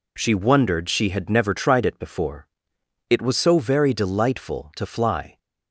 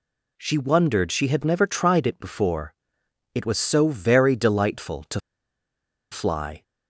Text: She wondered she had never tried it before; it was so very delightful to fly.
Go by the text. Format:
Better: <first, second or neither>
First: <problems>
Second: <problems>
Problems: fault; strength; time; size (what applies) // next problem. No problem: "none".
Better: first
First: none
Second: pauses between "to" and "fly"; noticeable; at 5.2 s; 0.92 s long